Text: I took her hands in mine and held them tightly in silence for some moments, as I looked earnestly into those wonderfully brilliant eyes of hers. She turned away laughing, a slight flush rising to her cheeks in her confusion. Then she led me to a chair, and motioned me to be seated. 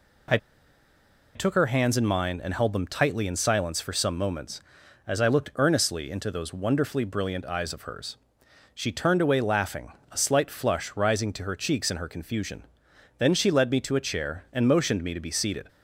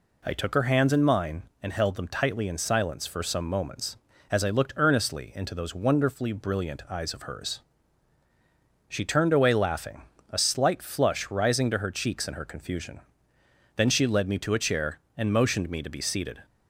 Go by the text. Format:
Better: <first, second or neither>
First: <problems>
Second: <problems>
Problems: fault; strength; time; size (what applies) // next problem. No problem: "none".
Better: second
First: pauses between "I" and "took"; at 0.3 s; 0.98 s long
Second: none